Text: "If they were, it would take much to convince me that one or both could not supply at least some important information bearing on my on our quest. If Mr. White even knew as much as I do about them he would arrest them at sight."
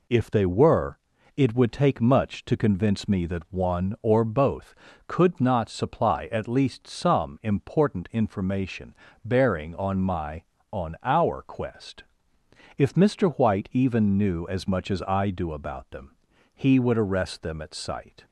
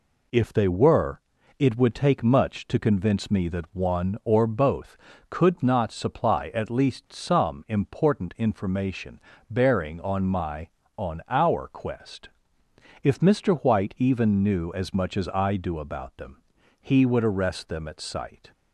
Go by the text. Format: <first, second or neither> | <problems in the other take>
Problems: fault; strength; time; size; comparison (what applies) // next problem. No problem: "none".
neither | pauses between "information" and "bearing"; slight; the same in both // pauses between "them" and "he"; the same in both